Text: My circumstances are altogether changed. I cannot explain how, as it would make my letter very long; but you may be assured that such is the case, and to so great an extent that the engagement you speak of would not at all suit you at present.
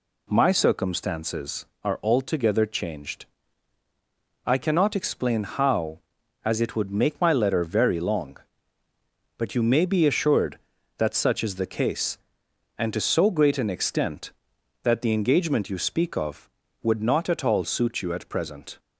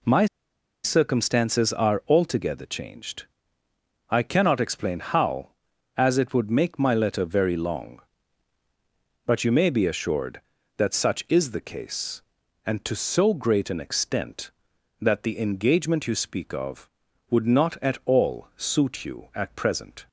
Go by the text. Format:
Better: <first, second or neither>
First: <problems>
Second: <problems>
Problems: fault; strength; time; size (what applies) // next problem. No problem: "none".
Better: first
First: none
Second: pauses between "My" and "circumstances"; noticeable; at 0.2 s; 0.58 s long